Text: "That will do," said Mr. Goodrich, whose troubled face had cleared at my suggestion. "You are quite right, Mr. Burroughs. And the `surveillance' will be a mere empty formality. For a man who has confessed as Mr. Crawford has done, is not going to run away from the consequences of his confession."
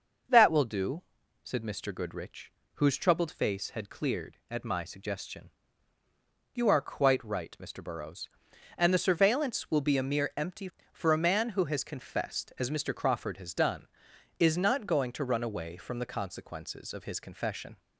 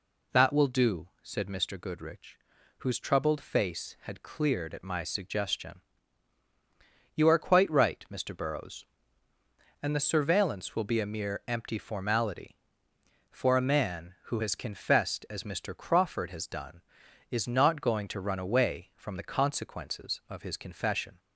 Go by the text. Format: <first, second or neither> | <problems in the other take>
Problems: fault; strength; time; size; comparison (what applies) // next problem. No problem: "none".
second | skips "formality"; at 10.7 s